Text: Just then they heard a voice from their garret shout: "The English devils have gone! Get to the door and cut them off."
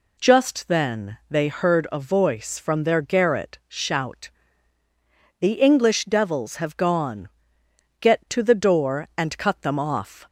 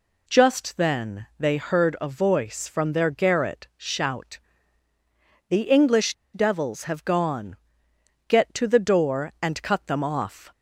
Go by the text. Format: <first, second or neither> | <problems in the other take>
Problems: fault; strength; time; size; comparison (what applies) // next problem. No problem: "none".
first | pauses between "English" and "devils"; slight; at 6.1 s; 0.19 s long